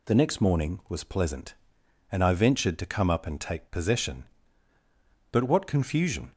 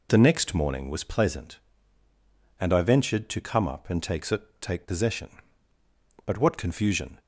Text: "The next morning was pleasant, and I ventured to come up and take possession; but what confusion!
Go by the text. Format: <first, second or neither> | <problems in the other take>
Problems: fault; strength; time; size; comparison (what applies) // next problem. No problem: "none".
first | says "take" twice; at 4.6 s